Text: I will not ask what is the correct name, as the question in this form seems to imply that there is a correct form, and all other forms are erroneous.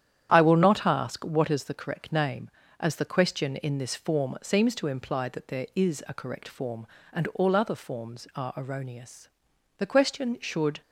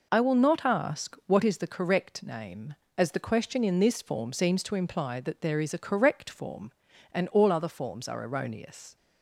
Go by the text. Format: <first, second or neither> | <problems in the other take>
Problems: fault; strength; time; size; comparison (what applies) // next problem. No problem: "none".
second | starts louder than the rest; strong; until 1.3 s; 10 dB // goes on to say "The question should"; noticeable; from 9.7 s on; 1.0 s long